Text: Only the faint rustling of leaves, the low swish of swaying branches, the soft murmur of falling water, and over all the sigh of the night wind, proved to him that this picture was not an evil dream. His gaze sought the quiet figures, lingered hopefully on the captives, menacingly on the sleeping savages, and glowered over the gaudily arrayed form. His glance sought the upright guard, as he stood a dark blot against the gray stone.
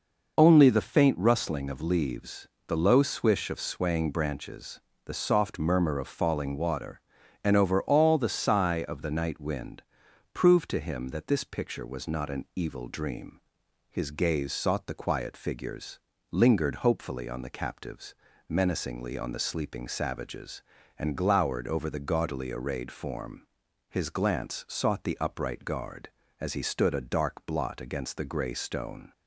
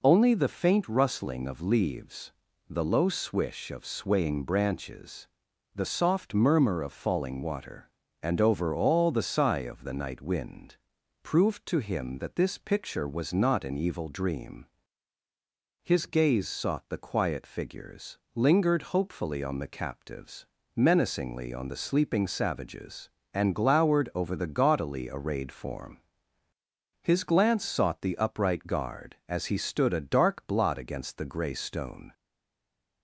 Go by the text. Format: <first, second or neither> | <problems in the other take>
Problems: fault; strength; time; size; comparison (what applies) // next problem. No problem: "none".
first | stays silent after the last word; slight; from 32.1 s on; 0.9 s long